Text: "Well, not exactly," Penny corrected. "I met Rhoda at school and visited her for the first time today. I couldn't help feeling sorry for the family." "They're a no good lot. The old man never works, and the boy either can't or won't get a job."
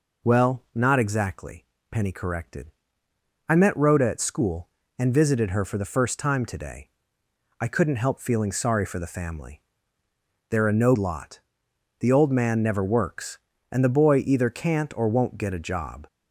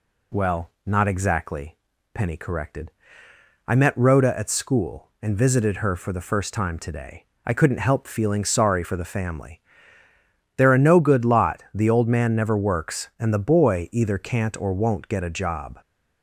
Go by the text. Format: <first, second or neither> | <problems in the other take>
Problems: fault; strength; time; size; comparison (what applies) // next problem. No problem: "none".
second | skips "good"; at 10.9 s